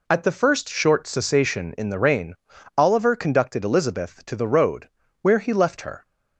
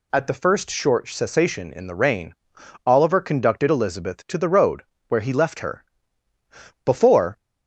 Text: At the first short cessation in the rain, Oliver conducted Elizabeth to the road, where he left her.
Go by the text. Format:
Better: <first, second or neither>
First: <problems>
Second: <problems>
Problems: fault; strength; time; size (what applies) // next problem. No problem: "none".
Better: first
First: none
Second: goes on to say "Before"; from 6.8 s on; 0.50 s long